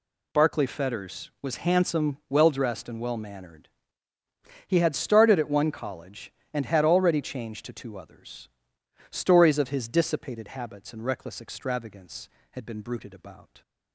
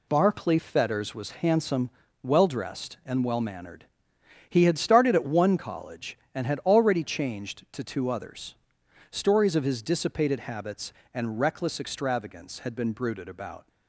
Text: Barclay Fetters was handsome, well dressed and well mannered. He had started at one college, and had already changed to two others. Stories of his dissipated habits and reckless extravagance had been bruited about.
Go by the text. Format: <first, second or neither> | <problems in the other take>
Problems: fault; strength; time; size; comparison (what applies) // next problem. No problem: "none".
neither | none